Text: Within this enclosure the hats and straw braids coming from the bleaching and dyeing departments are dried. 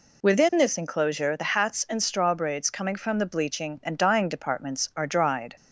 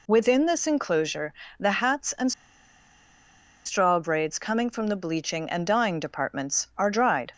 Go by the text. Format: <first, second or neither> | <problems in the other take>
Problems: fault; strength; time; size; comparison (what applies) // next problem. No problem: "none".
first | pauses between "enclosure" and "the"; slight; at 1.3 s; 0.26 s long // pauses between "and" and "straw"; strong; at 2.3 s; 1.3 s long